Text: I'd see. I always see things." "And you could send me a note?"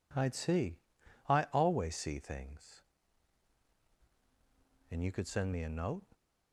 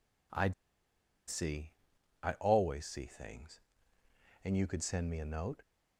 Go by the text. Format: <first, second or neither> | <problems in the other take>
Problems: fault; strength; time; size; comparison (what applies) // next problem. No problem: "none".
first | pauses between "I'd" and "see"; noticeable; at 0.5 s; 0.74 s long